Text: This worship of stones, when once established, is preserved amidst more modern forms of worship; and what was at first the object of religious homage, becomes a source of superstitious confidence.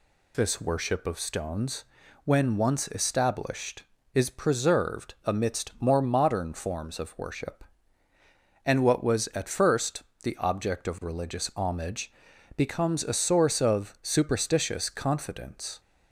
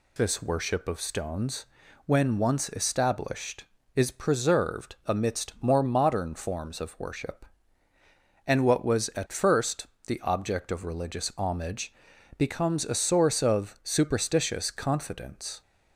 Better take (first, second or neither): neither